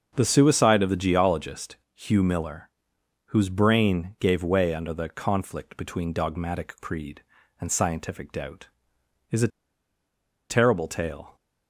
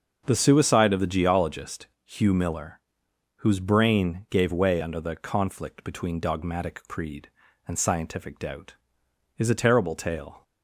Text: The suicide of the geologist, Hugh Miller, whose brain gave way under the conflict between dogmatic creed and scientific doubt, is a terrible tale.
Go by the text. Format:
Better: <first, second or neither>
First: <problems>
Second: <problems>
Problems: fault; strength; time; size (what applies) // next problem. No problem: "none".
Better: second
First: starts louder than the rest; until 1.1 s; 6.5 dB // pauses between "a" and "terrible"; at 9.4 s; 1.0 s long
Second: starts louder than the rest; until 1.2 s; 6.5 dB